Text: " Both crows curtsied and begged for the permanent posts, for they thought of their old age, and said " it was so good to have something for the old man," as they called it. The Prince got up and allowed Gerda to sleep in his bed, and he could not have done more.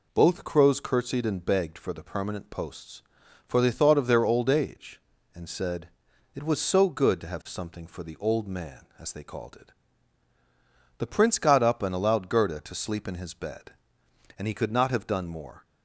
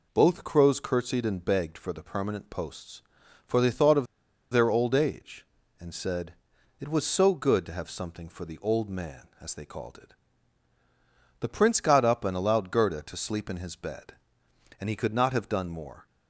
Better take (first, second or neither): first